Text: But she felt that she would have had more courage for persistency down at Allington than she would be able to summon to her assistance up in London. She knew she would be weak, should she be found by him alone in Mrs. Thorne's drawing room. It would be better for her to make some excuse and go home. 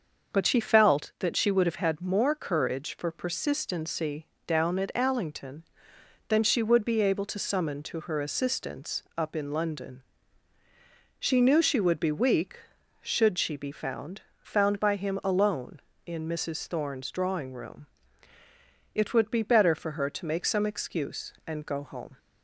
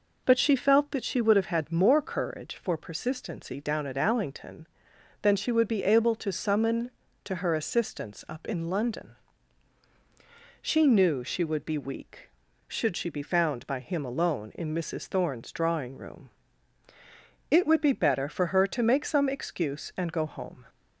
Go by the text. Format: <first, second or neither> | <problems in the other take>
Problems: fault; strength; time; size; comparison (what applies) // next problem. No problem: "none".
second | starts louder than the rest; until 1.3 s; 6.5 dB // pauses between "persistency" and "down"; slight; at 4.2 s; 0.20 s long // pauses between "assistance" and "up"; slight; at 9.0 s; 0.16 s long // says "found" twice; at 14.4 s